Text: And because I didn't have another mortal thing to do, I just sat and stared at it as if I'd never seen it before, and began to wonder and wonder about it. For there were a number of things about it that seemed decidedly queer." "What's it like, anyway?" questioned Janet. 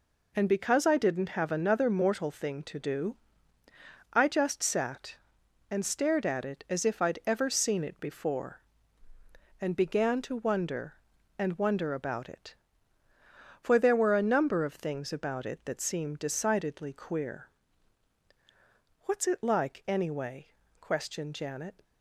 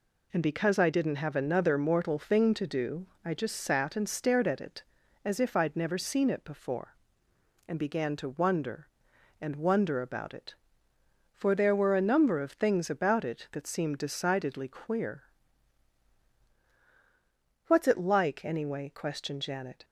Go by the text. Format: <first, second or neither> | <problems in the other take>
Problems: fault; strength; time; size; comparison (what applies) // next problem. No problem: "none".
second | says "ever" for "never"; at 7.2 s